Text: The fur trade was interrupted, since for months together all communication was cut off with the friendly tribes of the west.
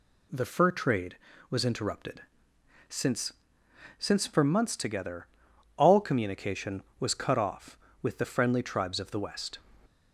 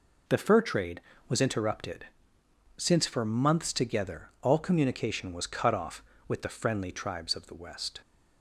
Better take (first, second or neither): second